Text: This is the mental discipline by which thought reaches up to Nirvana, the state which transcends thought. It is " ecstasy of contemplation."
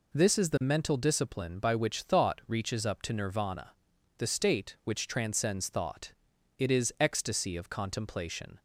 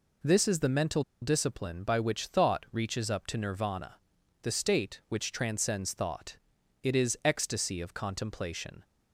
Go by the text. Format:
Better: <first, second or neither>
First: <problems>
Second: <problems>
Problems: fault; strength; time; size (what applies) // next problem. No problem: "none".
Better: first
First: none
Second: pauses between "mental" and "discipline"; slight; at 1.0 s; 0.20 s long